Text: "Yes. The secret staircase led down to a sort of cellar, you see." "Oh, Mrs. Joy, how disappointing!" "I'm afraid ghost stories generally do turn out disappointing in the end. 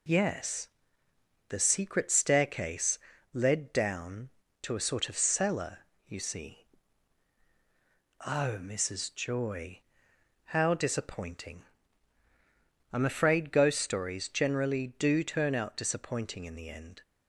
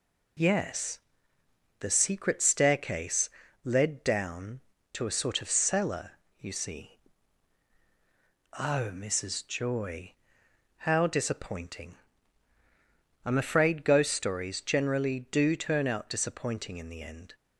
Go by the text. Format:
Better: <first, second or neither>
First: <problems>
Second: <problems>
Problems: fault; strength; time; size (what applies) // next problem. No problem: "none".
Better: neither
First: pauses between "staircase" and "led"; slight; at 2.9 s; 0.36 s long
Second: pauses between "staircase" and "led"; slight; at 3.2 s; 0.36 s long